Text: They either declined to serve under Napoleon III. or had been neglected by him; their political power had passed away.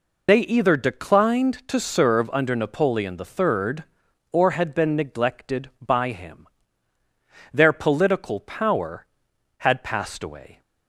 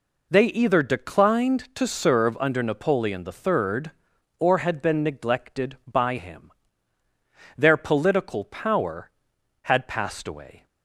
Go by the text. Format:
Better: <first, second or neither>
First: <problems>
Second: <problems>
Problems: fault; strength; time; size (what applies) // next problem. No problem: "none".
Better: second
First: loses the start of "They"; at 0.2 s; 45 ms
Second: none